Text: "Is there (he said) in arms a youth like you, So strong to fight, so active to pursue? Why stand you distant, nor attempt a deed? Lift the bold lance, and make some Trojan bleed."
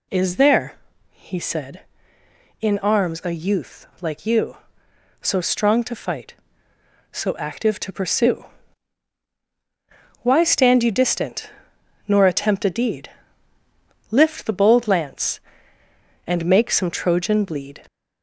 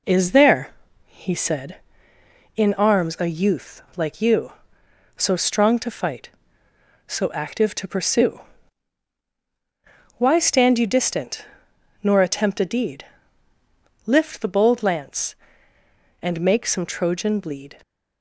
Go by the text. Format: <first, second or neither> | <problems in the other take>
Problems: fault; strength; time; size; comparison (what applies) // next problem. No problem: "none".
second | gets louder; slight; throughout; 3 dB